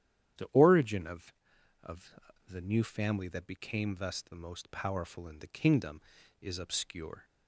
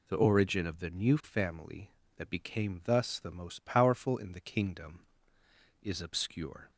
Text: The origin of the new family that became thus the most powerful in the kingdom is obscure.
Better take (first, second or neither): second